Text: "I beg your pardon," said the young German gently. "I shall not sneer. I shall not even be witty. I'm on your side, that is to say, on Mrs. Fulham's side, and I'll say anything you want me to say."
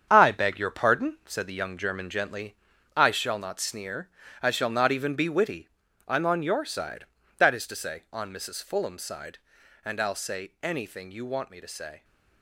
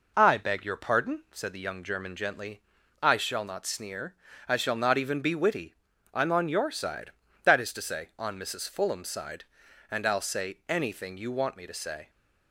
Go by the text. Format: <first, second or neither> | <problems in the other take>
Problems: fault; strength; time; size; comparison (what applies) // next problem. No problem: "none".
second | gets quieter; strong; throughout; 8.5 dB